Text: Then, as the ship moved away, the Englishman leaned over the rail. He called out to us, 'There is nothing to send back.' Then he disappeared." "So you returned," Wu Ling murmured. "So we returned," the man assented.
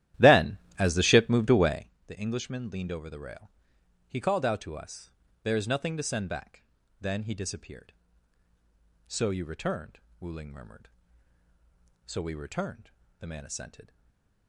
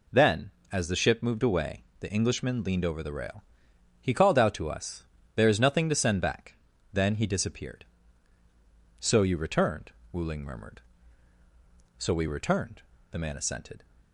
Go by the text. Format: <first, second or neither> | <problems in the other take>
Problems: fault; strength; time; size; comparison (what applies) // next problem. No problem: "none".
second | starts louder than the rest; strong; until 1.9 s; 13 dB // stays silent after the last word; slight; from 13.8 s on; 0.6 s long